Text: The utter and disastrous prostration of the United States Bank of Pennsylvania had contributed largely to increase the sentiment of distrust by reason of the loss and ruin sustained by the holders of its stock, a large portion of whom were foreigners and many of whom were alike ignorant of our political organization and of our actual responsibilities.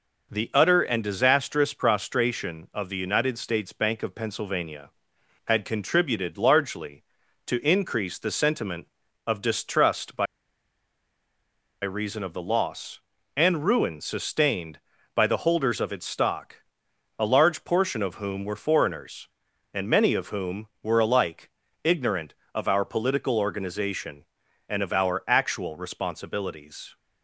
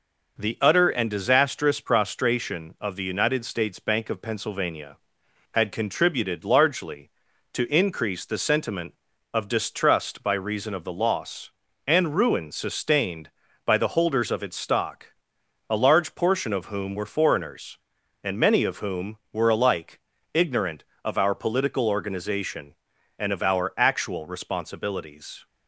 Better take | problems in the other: second | pauses between "by" and "reason"; strong; at 10.2 s; 1.5 s long // pauses between "alike" and "ignorant"; slight; at 21.4 s; 0.34 s long; slight in the second

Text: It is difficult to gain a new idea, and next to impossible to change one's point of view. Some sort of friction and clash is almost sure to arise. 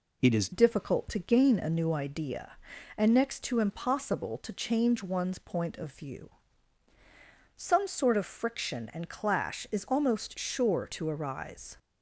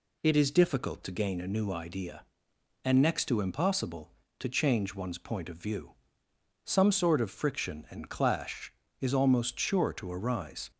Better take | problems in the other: second | changes voice at "difficult"; from 0.5 s on; 11.2 s long

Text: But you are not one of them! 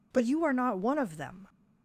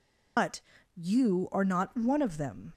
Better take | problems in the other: first | loses the start of "But"; at 0.3 s; 90 ms // pauses between "But" and "you"; slight; at 0.5 s; 0.36 s long

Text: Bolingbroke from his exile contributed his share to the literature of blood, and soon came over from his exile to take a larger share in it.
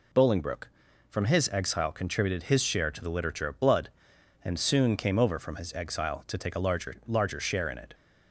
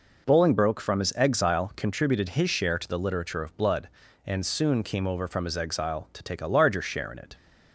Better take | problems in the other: second | says "larger" twice; at 7.0 s

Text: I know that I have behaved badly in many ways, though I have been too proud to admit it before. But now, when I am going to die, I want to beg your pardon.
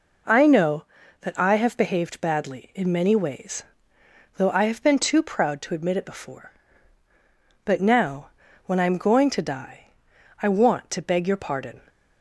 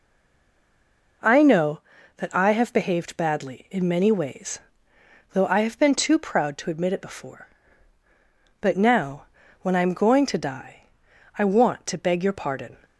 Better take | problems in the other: first | stays silent before the first word; noticeable; until 1.2 s; 1.2 s long

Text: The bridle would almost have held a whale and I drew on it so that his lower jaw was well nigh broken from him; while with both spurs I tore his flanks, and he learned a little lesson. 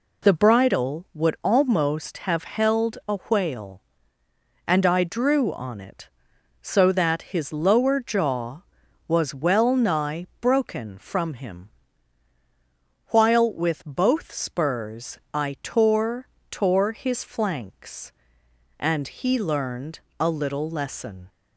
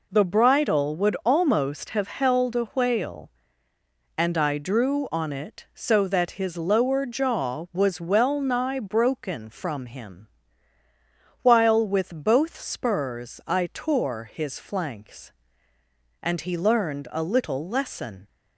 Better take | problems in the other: second | pauses between "spurs" and "I"; slight; at 15.1 s; 0.16 s long // says "tore" twice; at 16.4 s // pauses between "learned" and "a"; slight; at 19.9 s; 0.22 s long

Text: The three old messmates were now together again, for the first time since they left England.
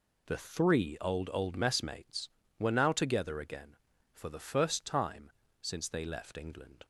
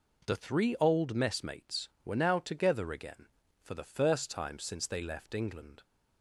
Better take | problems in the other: second | says "old" twice; at 1.3 s // pauses between "time" and "since"; slight; at 5.3 s; 0.28 s long

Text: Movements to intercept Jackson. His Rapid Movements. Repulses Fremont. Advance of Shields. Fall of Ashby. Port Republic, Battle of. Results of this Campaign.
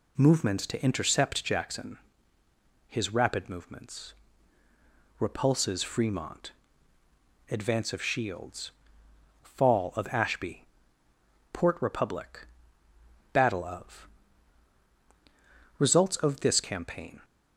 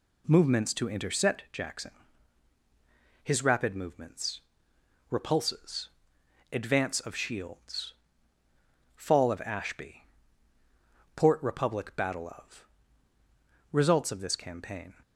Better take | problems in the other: first | skips "Fremont"; at 6.2 s

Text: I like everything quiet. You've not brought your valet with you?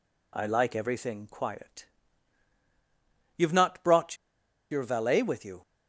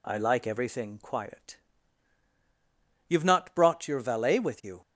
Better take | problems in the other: second | pauses between "brought" and "your"; noticeable; at 4.1 s; 0.55 s long

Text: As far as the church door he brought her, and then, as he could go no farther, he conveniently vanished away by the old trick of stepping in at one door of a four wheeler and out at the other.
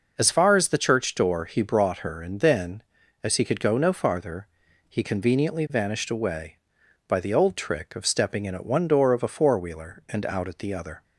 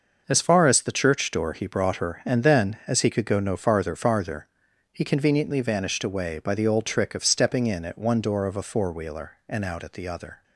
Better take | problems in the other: first | says "farther" twice; at 3.9 s

